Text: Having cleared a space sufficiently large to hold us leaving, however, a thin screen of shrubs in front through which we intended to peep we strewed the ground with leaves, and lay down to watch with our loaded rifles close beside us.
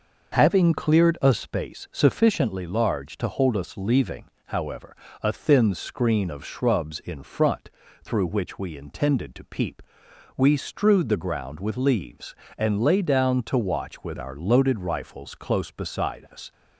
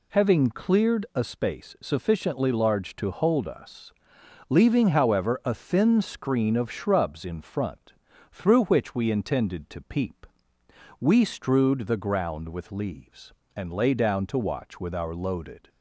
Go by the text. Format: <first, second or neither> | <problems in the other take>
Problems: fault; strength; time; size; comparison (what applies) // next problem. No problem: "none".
first | pauses between "us" and "leaving"; noticeable; at 3.9 s; 0.56 s long // pauses between "front" and "through"; at 7.9 s; 0.40 s long; slight in the first // pauses between "peep" and "we"; noticeable; at 10.2 s; 0.74 s long; noticeable in the first // stops before "rifles close beside us"; at 15.6 s